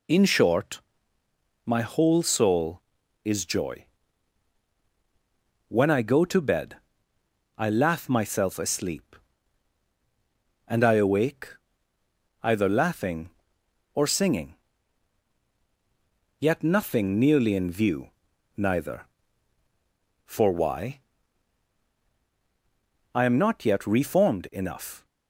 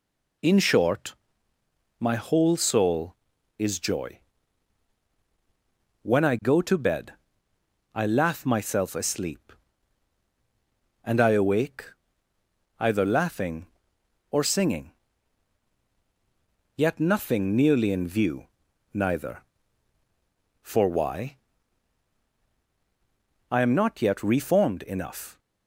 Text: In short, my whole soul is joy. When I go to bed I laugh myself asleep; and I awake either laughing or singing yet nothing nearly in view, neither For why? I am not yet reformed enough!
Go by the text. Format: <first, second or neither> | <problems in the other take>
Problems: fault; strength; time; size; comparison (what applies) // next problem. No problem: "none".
neither | pauses between "bed" and "I"; noticeable; the same in both // pauses between "awake" and "either"; noticeable; the same in both // pauses between "singing" and "yet"; strong; the same in both